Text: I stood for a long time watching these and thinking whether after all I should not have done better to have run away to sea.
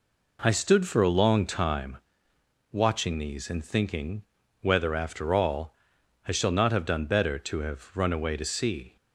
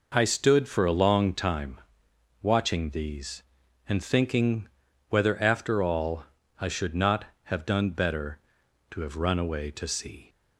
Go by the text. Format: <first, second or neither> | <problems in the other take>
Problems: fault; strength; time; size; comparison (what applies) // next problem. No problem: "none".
second | pauses between "time" and "watching"; noticeable; at 1.9 s; 0.74 s long; noticeable in the second // pauses between "thinking" and "whether"; at 4.2 s; 0.40 s long; also in the second // pauses between "all" and "I"; noticeable; at 5.7 s; 0.52 s long; slight in the second // says "shall" for "should"; at 6.3 s